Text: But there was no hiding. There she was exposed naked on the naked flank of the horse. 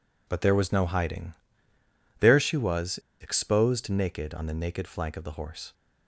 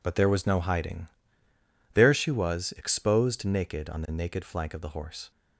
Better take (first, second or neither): second